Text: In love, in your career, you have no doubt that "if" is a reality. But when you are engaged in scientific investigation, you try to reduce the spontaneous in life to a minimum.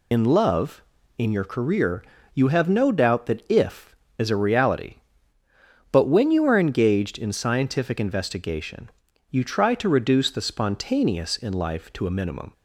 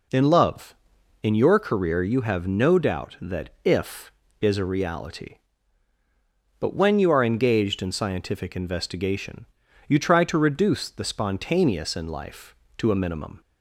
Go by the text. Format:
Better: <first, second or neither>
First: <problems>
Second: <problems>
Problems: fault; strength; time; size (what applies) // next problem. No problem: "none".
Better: second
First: loses the start of "In"; at 0.1 s; 70 ms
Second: none